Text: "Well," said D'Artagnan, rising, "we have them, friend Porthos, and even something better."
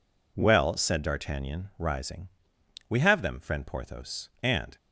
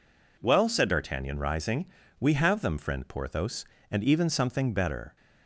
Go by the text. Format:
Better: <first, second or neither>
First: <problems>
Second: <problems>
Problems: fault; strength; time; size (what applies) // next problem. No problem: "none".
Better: second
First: stops before "even something better"; at 4.7 s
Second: none